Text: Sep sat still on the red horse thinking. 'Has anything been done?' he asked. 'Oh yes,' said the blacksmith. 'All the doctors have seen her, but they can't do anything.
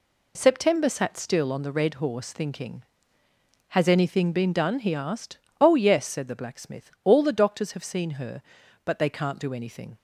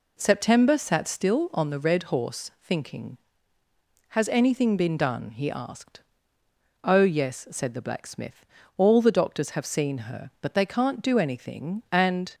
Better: first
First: none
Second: goes on to say "And"; slight; from 11.9 s on; 0.42 s long

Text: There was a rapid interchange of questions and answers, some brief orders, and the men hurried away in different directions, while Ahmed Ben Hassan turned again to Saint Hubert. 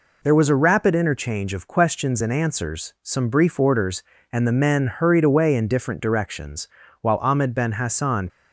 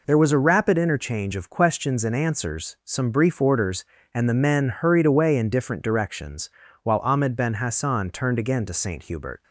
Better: second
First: stops before "turned again to Saint Hubert"; at 8.2 s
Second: none

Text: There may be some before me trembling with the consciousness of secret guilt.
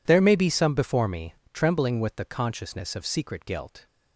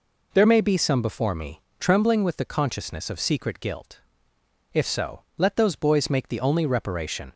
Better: first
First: pauses between "me" and "trembling"; slight; at 1.3 s; 0.18 s long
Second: pauses between "me" and "trembling"; slight; at 1.6 s; 0.20 s long // goes on to say "If so let those boys make the only reparation"; strong; from 4.7 s on; 2.6 s long

